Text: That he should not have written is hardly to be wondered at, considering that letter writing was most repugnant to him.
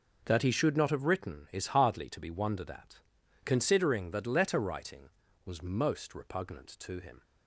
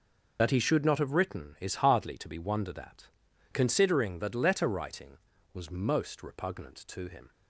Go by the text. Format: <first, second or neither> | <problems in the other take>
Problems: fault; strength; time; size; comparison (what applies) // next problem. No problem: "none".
first | loses the start of "That"; at 0.3 s; 95 ms